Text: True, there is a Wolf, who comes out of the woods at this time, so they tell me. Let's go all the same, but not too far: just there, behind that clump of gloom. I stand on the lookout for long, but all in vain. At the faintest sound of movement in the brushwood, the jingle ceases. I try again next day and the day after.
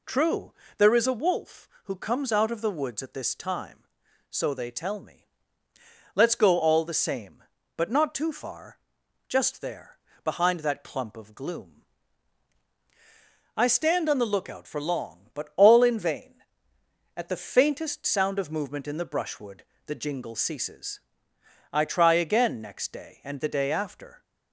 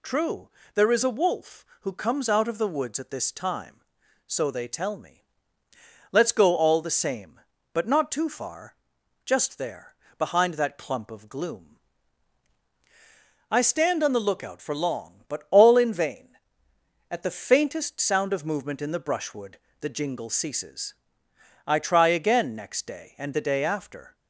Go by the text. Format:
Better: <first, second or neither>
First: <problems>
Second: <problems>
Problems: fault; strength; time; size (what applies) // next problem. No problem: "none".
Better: second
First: starts louder than the rest; slight; until 1.1 s; 3 dB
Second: none